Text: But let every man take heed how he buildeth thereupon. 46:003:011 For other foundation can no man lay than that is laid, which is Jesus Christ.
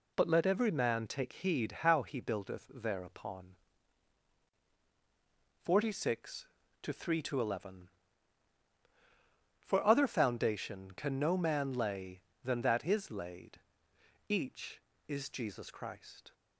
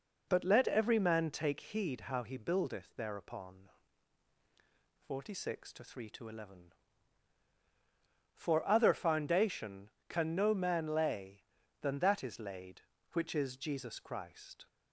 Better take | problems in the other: second | says "each" for "which"; at 14.2 s

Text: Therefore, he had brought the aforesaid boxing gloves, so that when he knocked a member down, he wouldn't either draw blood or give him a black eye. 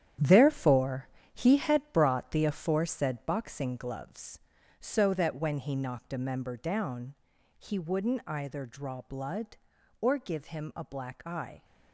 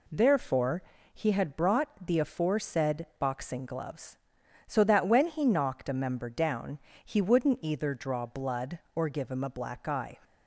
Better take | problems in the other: second | gets quieter; strong; throughout; 9.5 dB

